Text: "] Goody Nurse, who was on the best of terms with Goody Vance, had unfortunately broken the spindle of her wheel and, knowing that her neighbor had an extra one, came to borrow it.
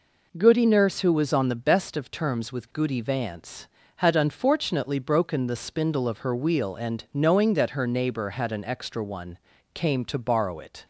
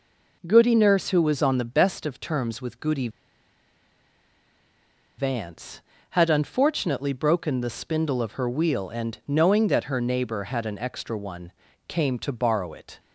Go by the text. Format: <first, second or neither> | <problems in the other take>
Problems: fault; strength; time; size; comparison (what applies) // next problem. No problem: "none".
first | pauses between "Goody" and "Vance"; strong; at 3.0 s; 2.0 s long